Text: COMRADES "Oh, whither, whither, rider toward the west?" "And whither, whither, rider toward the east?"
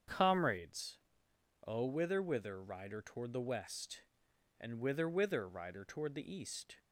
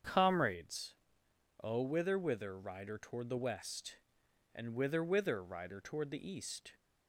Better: neither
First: starts louder than the rest; strong; until 1.7 s; 7.5 dB // pauses between "COMRADES" and "Oh"; noticeable; at 0.9 s; 0.70 s long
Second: starts louder than the rest; strong; until 1.7 s; 7.5 dB // pauses between "COMRADES" and "Oh"; noticeable; at 0.9 s; 0.70 s long

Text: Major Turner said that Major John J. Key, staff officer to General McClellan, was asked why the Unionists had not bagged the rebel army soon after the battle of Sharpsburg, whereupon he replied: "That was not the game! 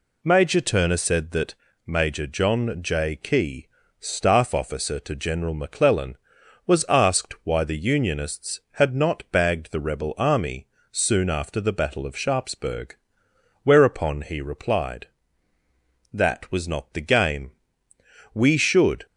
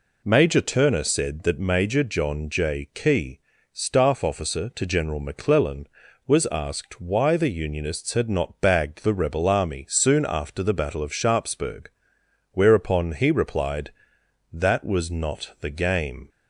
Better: second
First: pauses between "that" and "Major"; slight; at 1.5 s; 0.32 s long // pauses between "army" and "soon"; slight; at 10.6 s; 0.24 s long // goes on to say "We should"; noticeable; from 18.3 s on; 0.72 s long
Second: none

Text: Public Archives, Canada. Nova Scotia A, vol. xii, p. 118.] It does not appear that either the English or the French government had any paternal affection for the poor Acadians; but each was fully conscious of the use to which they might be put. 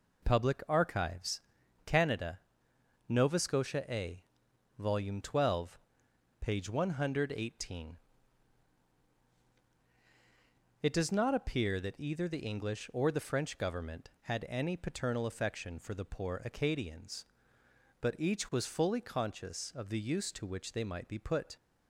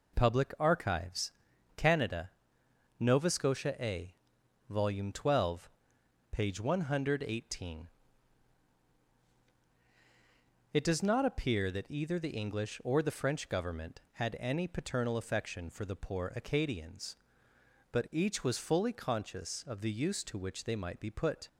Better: neither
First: none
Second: none

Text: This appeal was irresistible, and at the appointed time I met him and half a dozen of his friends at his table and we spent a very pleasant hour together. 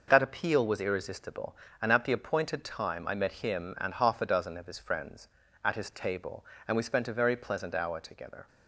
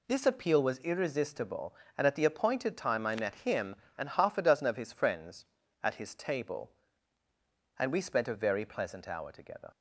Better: second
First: says "That" for "This"; at 0.0 s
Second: none

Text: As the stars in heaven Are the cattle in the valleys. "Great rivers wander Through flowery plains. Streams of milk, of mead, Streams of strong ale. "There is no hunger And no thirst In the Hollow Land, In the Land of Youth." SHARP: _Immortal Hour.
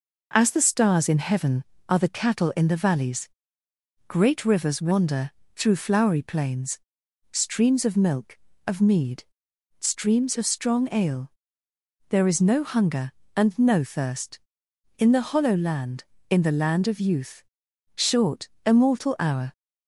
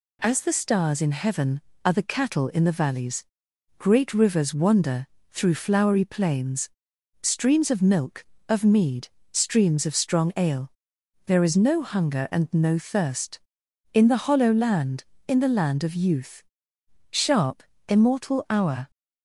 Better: second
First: pauses between "wander" and "Through"; slight; at 5.2 s; 0.26 s long // says "Short" for "SHARP"; at 17.9 s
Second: pauses between "wander" and "Through"; slight; at 5.0 s; 0.26 s long

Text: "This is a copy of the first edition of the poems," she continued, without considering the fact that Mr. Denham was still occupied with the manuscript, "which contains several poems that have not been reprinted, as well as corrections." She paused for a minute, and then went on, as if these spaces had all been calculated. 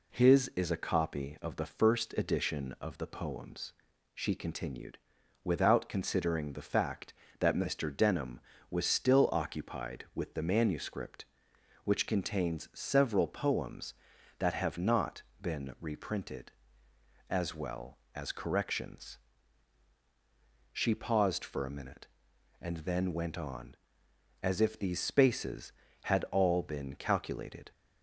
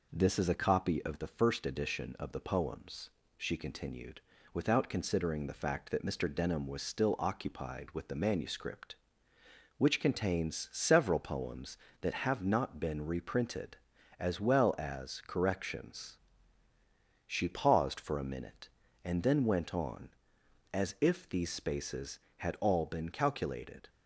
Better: second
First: says "His" for "This"; at 0.1 s // pauses between "not" and "been"; slight; at 15.2 s; 0.18 s long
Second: none

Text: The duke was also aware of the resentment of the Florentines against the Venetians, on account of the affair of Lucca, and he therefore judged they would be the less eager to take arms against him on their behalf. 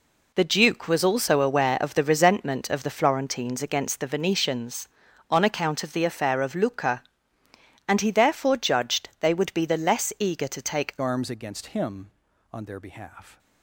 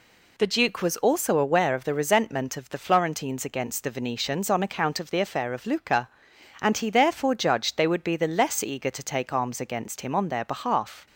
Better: second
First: changes voice at "arms"; from 11.0 s on; 2.3 s long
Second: none

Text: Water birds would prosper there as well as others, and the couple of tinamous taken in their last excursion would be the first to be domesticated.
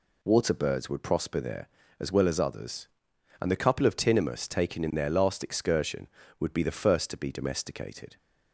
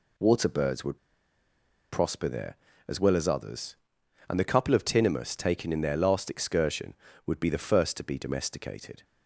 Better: first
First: none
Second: pauses between "would" and "prosper"; noticeable; at 0.9 s; 0.95 s long

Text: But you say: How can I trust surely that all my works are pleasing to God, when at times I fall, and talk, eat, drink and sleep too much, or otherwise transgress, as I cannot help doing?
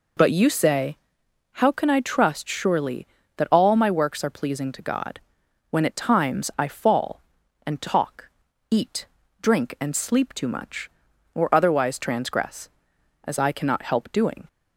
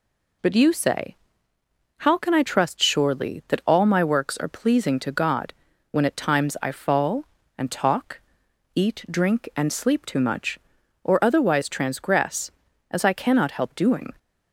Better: neither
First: none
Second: none

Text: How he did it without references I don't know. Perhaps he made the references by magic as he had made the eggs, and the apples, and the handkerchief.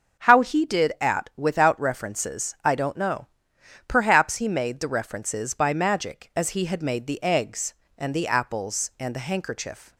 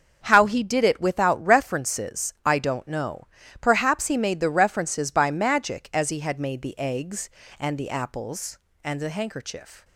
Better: second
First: starts louder than the rest; until 1.2 s; 6 dB // says "at" for "it"; at 0.9 s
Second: starts louder than the rest; until 1.2 s; 7 dB

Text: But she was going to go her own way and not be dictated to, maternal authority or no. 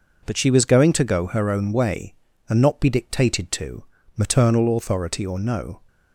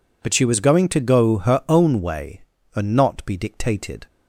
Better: first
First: none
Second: stops before "to maternal authority or no"; at 4.0 s

